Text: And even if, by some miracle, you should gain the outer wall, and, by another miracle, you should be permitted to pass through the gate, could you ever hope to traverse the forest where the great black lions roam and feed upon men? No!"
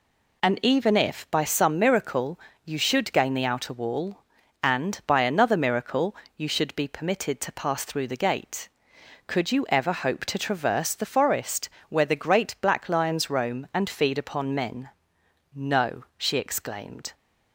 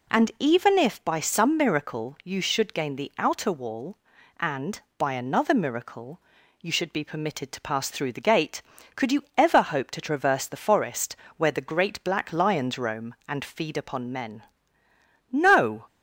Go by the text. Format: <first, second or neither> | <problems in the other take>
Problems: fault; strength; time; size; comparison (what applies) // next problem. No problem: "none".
second | pauses between "forest" and "where"; slight; at 11.6 s; 0.22 s long; slight in the second // goes on to say "she exclaimed"; noticeable; from 16.1 s on; 0.96 s long